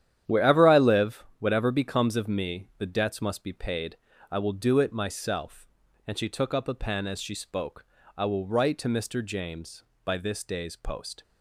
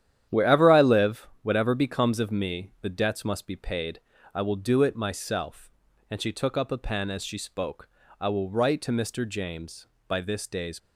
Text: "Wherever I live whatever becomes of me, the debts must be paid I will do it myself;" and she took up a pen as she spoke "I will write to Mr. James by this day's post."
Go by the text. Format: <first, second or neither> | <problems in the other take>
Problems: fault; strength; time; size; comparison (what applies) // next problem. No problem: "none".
first | starts louder than the rest; strong; until 1.4 s; 10.5 dB; strong in the first // pauses between "live" and "whatever"; slight; at 1.2 s; 0.16 s long; slight in the first // pauses between "paid" and "I"; slight; at 3.9 s; 0.32 s long; slight in the first // pauses between "spoke" and "I"; slight; at 7.8 s; 0.30 s long; slight in the first // stops before "post"; at 10.7 s